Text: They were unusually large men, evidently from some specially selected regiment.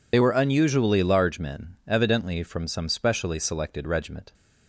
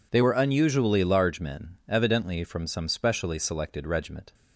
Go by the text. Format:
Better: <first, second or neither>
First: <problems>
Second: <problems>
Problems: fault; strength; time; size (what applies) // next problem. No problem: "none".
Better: second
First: loses the start of "They"; at 0.1 s; 45 ms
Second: none